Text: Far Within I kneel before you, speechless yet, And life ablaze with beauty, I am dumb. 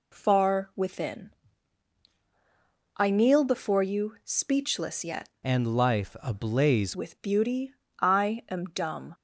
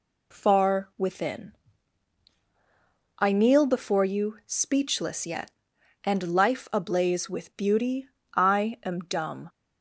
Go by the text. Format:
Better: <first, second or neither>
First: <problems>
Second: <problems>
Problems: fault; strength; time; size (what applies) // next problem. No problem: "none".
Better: second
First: pauses between "Within" and "I"; strong; at 1.3 s; 1.6 s long // changes voice from "And" to "ablaze"; from 5.4 to 6.9 s; 1.5 s long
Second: pauses between "Within" and "I"; strong; at 1.5 s; 1.6 s long